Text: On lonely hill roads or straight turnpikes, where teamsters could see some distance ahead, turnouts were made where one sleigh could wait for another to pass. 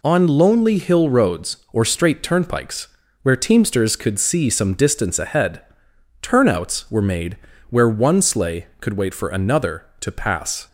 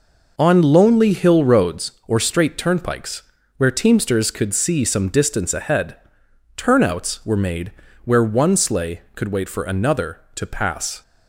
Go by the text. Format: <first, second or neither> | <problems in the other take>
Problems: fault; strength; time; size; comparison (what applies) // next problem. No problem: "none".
first | starts louder than the rest; noticeable; until 1.8 s; 5 dB // pauses between "made" and "where"; slight; at 7.6 s; 0.36 s long; slight in the first